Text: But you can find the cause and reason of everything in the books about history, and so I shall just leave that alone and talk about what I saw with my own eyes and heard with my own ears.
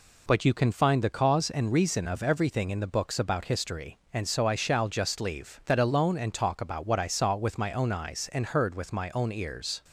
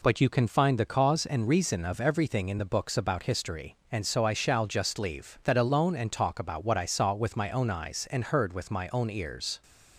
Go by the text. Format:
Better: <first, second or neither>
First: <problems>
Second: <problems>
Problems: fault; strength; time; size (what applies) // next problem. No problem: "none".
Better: neither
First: none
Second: none